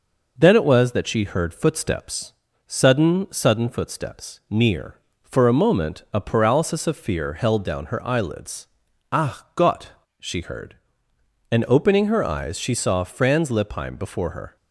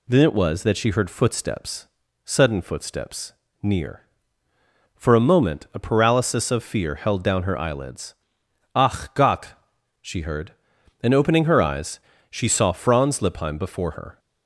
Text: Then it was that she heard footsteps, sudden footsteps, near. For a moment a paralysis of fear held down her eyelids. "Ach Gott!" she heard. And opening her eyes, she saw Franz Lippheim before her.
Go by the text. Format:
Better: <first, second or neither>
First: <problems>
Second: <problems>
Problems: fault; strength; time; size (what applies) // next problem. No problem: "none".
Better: second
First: says "sudden" twice; at 3.2 s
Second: none